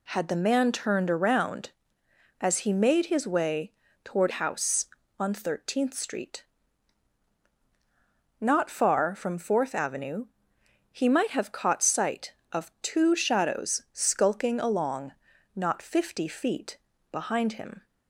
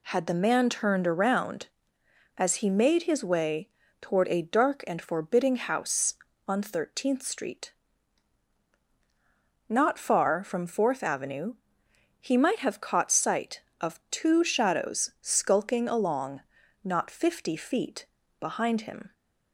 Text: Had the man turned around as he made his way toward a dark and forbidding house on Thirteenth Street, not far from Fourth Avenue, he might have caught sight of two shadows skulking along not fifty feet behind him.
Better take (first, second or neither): second